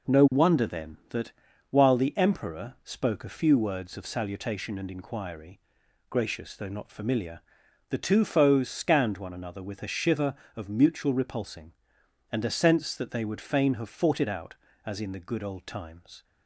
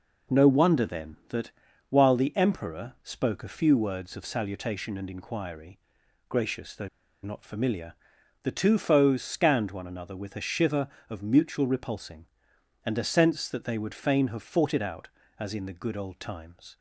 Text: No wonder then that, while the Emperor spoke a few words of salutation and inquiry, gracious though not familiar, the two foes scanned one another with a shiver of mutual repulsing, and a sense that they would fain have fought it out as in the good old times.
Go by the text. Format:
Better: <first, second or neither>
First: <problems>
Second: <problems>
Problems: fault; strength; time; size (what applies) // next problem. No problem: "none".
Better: first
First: none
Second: pauses between "though" and "not"; slight; at 6.8 s; 0.34 s long